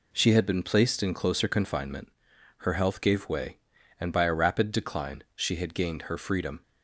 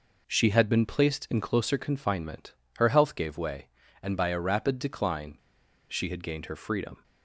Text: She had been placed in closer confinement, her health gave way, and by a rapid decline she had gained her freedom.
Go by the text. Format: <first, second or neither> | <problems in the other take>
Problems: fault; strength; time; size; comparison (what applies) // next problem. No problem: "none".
first | pauses between "decline" and "she"; noticeable; at 5.3 s; 0.52 s long